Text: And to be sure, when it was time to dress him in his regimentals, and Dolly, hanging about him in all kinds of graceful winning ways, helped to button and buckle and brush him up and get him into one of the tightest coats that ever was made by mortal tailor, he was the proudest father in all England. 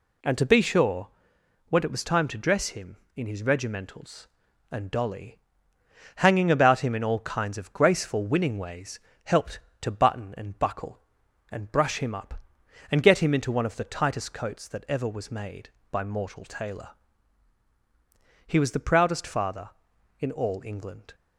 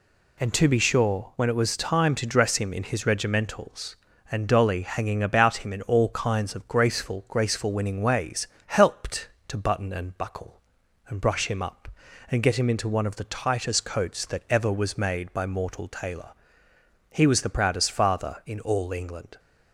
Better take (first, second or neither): first